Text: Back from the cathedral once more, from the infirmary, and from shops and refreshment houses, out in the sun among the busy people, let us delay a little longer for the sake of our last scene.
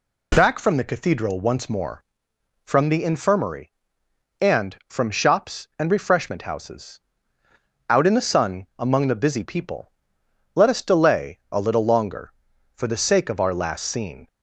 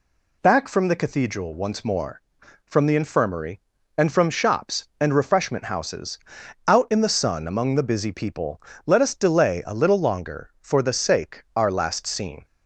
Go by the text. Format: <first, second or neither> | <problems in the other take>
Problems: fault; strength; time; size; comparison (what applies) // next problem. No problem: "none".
first | skips "of"; at 11.4 s